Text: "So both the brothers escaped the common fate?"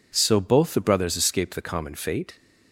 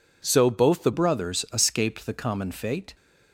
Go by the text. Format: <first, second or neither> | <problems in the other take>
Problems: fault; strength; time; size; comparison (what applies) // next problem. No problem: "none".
first | changes voice at "brothers"; from 0.9 s on; 2.0 s long